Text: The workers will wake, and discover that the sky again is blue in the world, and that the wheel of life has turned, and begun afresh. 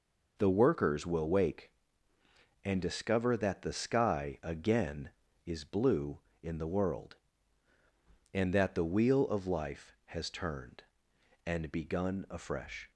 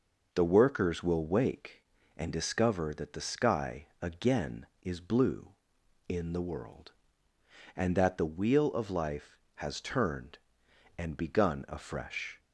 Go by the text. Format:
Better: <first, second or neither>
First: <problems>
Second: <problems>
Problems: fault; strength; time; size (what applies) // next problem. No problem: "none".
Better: neither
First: none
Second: none